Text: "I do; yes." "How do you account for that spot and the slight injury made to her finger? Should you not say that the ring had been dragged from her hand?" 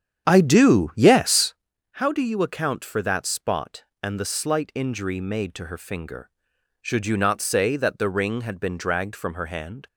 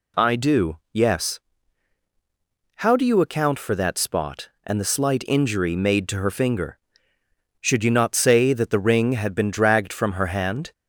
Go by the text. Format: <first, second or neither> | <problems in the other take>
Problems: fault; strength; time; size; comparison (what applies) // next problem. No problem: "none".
second | starts louder than the rest; strong; until 1.5 s; 9 dB